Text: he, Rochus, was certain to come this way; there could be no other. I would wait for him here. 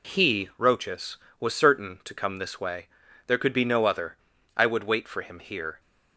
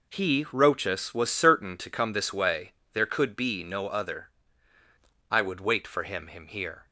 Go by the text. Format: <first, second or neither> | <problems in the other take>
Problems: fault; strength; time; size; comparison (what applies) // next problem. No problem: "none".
first | says "him" twice; at 6.2 s